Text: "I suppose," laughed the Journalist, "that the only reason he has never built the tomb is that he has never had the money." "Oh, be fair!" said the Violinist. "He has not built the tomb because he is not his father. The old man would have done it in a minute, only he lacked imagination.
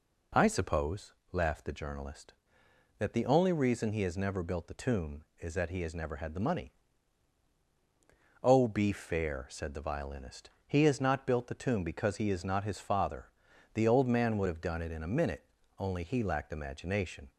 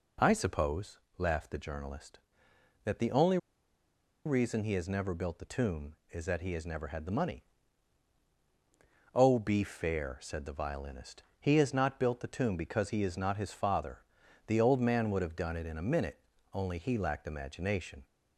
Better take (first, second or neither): first